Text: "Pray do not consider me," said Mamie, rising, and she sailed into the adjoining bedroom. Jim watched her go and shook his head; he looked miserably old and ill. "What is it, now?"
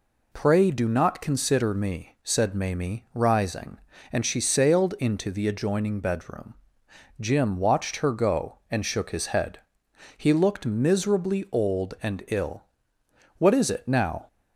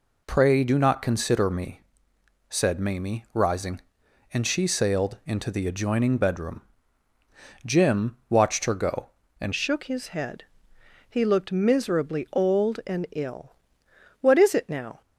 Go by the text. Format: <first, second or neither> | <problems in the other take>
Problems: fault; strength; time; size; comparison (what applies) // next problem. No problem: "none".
first | changes voice at "shook"; from 9.5 s on; 5.5 s long